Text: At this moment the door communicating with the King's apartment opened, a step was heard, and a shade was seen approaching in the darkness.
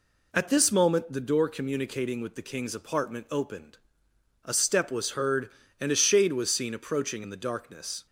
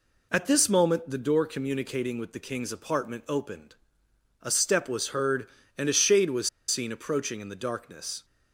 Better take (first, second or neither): first